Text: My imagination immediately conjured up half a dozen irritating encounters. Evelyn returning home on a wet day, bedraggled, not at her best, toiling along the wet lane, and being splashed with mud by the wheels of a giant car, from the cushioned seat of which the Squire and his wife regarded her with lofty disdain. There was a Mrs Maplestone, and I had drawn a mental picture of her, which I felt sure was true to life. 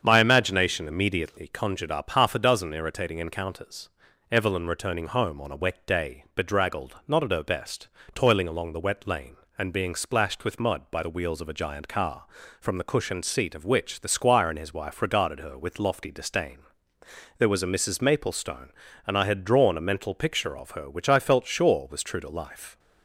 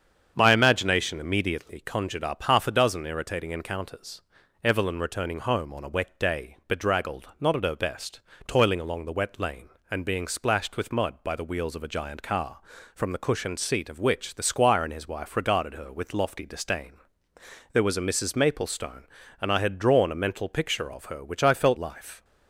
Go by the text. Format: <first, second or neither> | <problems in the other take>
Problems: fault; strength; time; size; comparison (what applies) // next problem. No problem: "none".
first | starts louder than the rest; strong; until 1.3 s; 7.5 dB; strong in the first // skips "sure was true to"; at 21.7 s